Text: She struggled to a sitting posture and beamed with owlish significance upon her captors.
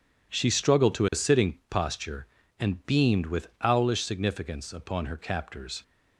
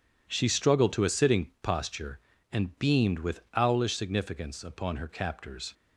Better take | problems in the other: neither | none

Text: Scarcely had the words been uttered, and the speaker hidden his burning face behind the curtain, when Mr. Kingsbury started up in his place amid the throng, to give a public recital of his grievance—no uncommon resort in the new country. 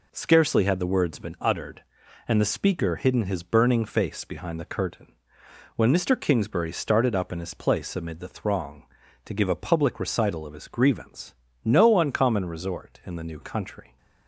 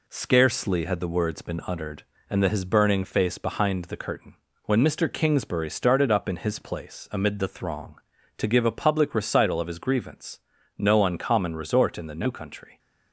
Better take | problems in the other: first | skips "speaker hidden"; at 2.4 s

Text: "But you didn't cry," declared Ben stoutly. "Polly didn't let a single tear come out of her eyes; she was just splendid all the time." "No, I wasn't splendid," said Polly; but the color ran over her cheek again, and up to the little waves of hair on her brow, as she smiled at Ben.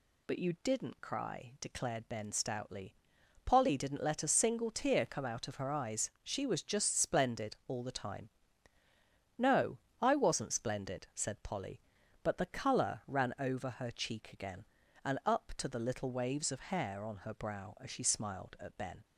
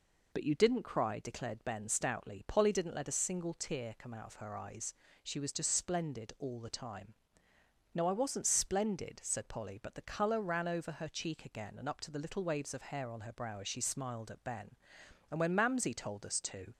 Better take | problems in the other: first | goes on to say "And when Mamsie told us to"; from 15.3 s on; 1.4 s long

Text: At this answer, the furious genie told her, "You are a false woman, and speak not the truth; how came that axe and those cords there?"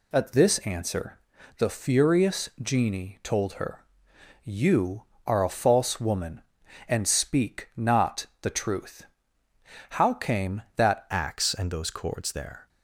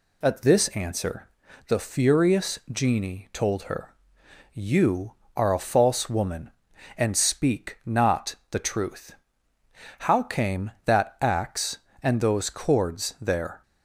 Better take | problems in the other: second | pauses between "not" and "the"; slight; at 8.2 s; 0.16 s long; slight in the second // changes voice at "axe"; from 11.1 s on; 1.5 s long

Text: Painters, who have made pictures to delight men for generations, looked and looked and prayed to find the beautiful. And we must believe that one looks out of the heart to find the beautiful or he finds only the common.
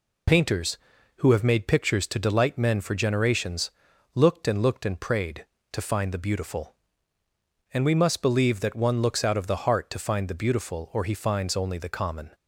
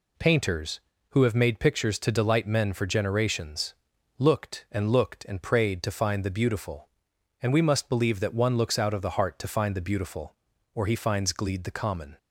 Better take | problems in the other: first | says "gleed" for "only"; at 11.3 s

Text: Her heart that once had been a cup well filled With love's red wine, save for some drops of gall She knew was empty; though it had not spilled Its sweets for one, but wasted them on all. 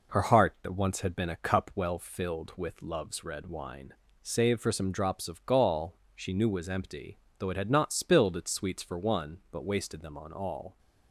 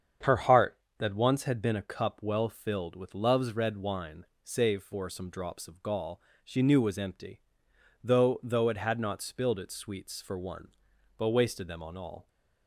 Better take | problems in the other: first | starts louder than the rest; strong; until 1.4 s; 7.5 dB // pauses between "gall" and "She"; slight; at 6.1 s; 0.26 s long; slight in the first // says "though" twice; at 8.4 s

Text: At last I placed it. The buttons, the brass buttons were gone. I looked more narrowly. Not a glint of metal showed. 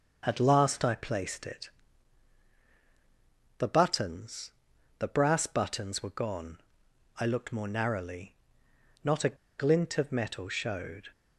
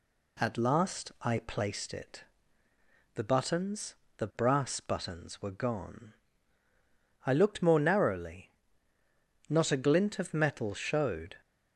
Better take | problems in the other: second | starts louder than the rest; until 1.2 s; 6 dB // pauses between "a" and "glint"; slight; at 9.3 s; 0.24 s long

